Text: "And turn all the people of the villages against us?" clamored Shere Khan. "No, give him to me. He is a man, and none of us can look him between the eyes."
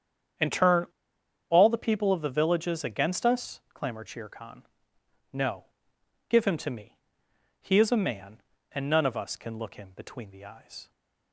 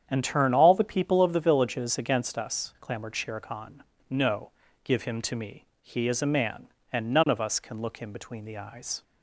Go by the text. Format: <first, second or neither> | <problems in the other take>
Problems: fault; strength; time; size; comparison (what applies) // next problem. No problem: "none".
second | starts louder than the rest; strong; until 2.0 s; 8 dB; strong in the second // pauses between "turn" and "all"; noticeable; at 0.8 s; 0.63 s long